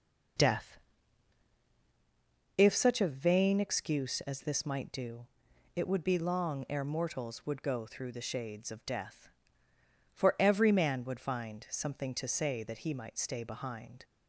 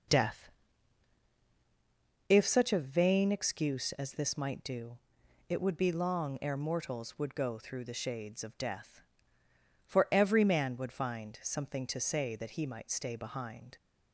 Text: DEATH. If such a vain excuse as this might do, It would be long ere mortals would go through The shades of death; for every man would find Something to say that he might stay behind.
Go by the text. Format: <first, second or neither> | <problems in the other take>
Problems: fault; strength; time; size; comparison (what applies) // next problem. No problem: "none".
neither | none